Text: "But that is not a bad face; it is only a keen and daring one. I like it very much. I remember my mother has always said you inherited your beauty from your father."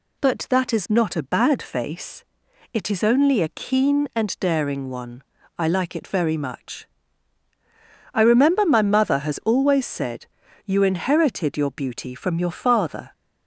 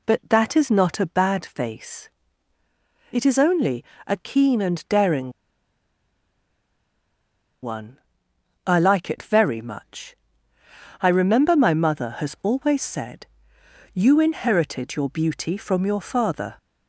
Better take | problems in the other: first | pauses between "only" and "a"; slight; at 3.8 s; 0.20 s long // pauses between "daring" and "one"; strong; at 5.3 s; 2.3 s long // pauses between "said" and "you"; noticeable; at 13.2 s; 0.64 s long; also in the first

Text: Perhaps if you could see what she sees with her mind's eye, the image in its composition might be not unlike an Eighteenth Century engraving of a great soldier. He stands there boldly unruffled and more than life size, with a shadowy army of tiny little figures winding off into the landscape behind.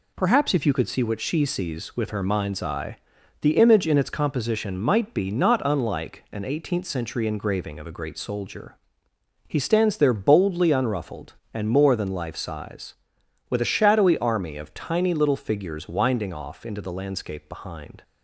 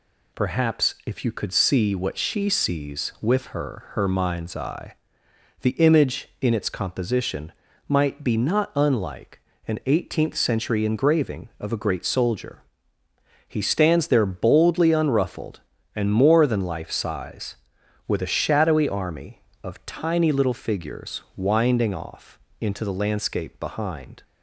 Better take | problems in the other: first | says "her" twice; at 3.9 s // pauses between "composition" and "might"; slight; at 7.5 s; 0.34 s long // pauses between "unlike" and "an"; slight; at 9.4 s; 0.28 s long // pauses between "figures" and "winding"; slight; at 21.2 s; 0.16 s long // pauses between "off" and "into"; slight; at 22.3 s; 0.22 s long

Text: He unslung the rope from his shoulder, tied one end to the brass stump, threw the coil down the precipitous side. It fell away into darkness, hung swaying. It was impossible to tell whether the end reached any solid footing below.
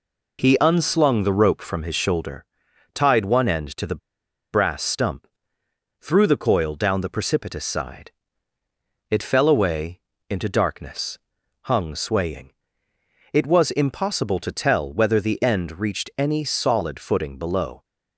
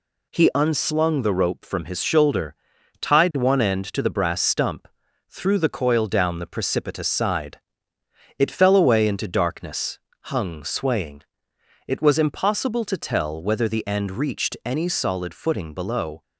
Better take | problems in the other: second | pauses between "the" and "brass"; noticeable; at 3.9 s; 0.52 s long // pauses between "away" and "into"; slight; at 10.0 s; 0.28 s long

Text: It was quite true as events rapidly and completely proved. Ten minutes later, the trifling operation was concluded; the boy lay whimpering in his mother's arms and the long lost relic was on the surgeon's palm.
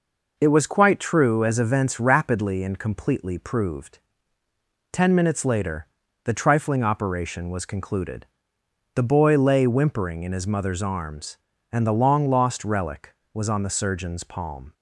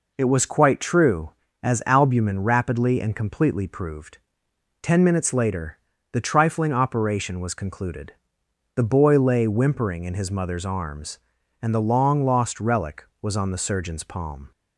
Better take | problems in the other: first | says "albumin" for "events"; at 1.8 s

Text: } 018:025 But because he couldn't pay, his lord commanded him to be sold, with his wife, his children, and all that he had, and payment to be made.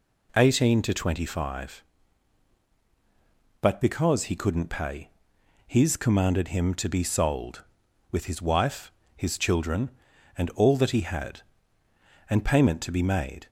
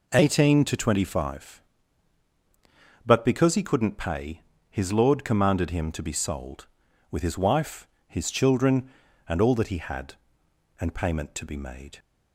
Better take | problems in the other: second | skips "lord"; at 5.9 s

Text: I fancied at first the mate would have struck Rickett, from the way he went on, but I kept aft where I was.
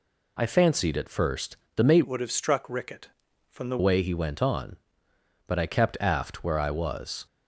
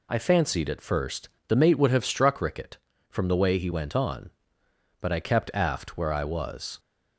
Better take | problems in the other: second | pauses between "first" and "the"; slight; at 1.5 s; 0.18 s long; slight in the second // changes voice from "would" to "the"; from 2.0 to 3.7 s; 1.7 s long

